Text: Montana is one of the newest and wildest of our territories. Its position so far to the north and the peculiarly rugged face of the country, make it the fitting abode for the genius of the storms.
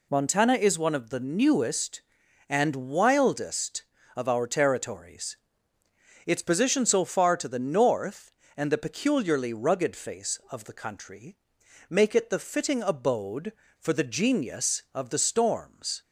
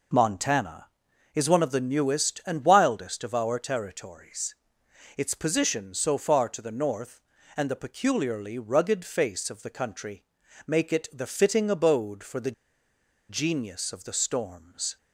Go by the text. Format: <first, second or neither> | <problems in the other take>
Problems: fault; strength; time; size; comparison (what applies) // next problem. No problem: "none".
first | pauses between "the" and "genius"; noticeable; at 12.5 s; 0.77 s long